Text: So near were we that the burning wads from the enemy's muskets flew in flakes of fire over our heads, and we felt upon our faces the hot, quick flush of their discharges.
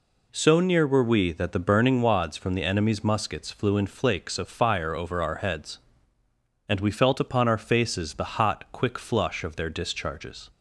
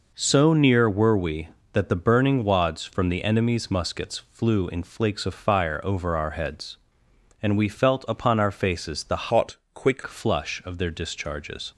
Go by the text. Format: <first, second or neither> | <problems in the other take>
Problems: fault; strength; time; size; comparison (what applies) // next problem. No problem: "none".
first | changes voice from "hot" to "quick"; from 9.3 to 10.0 s; 0.7 s long